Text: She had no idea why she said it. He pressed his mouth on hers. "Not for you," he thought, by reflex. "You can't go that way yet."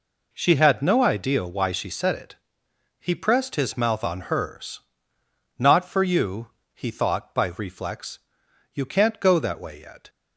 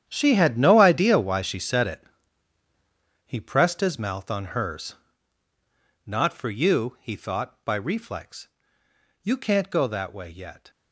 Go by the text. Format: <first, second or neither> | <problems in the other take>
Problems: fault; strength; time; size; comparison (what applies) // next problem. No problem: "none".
first | gets quieter; strong; throughout; 15.5 dB